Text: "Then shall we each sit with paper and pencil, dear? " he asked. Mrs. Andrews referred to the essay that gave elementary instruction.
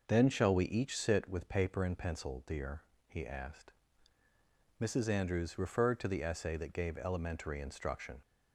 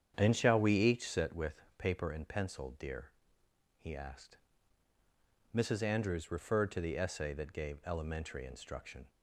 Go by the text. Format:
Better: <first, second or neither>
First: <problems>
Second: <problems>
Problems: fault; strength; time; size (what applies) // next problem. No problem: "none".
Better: first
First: none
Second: starts louder than the rest; strong; until 1.3 s; 8.5 dB // pauses between "with" and "paper"; slight; at 1.6 s; 0.16 s long